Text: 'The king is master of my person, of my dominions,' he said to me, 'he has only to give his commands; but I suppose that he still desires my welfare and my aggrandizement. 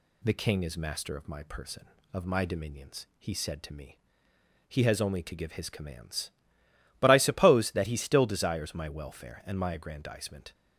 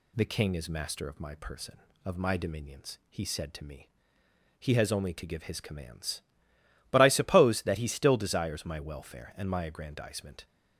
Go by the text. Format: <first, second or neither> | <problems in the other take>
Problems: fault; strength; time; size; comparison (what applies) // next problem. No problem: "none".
neither | none